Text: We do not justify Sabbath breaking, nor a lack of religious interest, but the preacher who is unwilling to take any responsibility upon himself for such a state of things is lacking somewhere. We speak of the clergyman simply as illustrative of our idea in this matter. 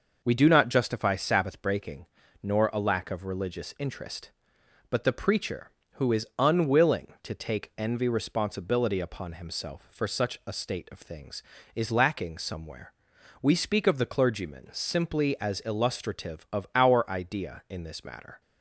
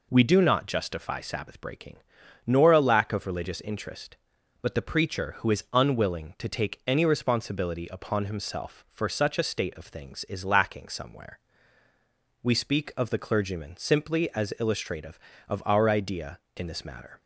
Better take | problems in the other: second | says "envy" for "any"; at 7.7 s

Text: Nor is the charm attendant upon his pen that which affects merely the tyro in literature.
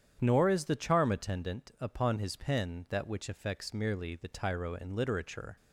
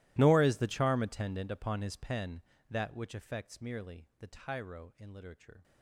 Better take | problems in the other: first | gets quieter; strong; throughout; 24 dB // starts louder than the rest; strong; until 1.1 s; 16.5 dB; strong in the first

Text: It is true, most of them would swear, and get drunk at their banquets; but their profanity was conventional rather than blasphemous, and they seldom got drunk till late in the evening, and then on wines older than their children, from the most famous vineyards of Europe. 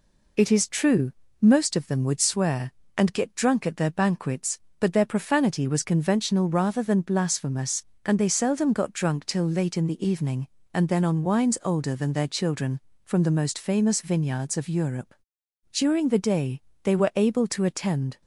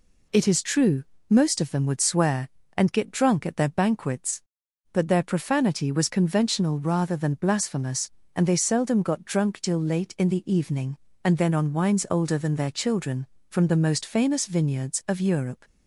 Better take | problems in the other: second | goes on to say "During the day they were able to attend"; strong; from 15.7 s on; 2.4 s long

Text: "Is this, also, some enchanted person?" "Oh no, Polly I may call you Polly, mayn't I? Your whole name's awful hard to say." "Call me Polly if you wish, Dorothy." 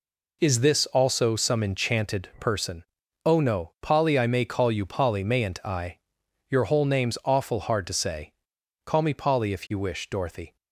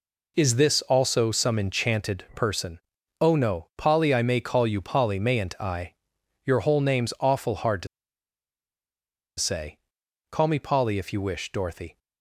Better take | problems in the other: first | pauses between "to" and "say"; strong; at 7.8 s; 1.5 s long

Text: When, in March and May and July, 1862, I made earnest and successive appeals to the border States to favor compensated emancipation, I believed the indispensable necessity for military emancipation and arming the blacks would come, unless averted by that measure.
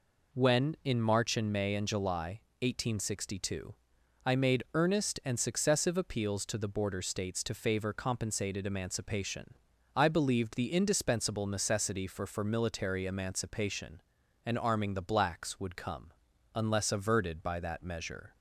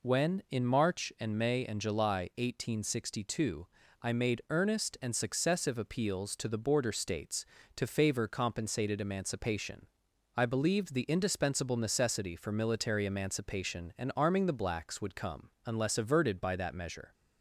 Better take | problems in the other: second | says "for" twice; at 12.2 s

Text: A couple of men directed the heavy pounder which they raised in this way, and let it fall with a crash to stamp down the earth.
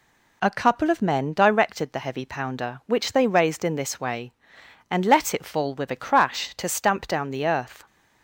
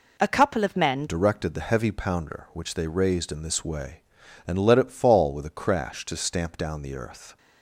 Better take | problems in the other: first | changes voice at "directed"; from 1.0 s on; 6.3 s long

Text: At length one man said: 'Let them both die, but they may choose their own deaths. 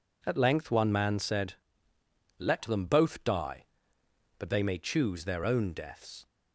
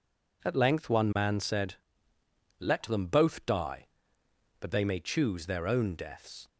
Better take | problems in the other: neither | none

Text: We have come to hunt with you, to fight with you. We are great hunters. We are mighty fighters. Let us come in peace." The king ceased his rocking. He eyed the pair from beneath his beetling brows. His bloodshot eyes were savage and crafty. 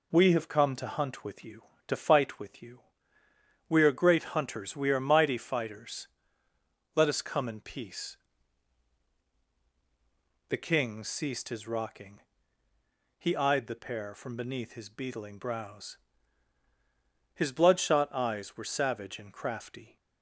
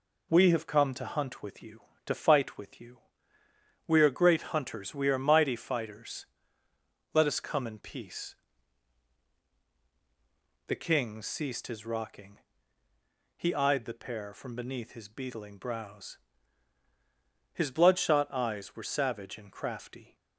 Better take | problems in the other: neither | none

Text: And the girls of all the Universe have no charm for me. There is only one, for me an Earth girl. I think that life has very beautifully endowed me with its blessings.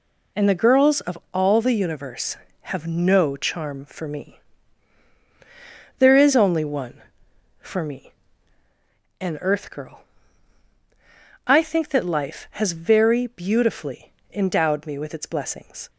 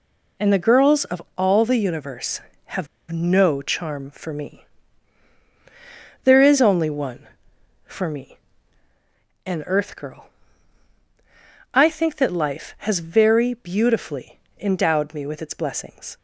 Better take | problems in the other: first | pauses between "of" and "all"; slight; at 1.2 s; 0.16 s long; slight in the first // pauses between "have" and "no"; slight; at 2.8 s; 0.24 s long // pauses between "me" and "an"; at 8.3 s; 1.1 s long; also in the first // pauses between "beautifully" and "endowed"; slight; at 14.3 s; 0.20 s long; slight in the first

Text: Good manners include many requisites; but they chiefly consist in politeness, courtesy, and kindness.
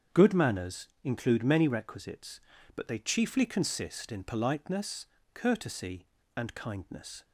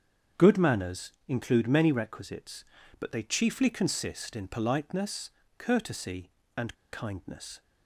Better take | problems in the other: first | starts louder than the rest; strong; until 1.5 s; 7.5 dB; strong in the first // pauses between "manners" and "include"; slight; at 1.1 s; 0.16 s long; slight in the first // pauses between "and" and "kindness"; slight; at 6.7 s; 0.16 s long

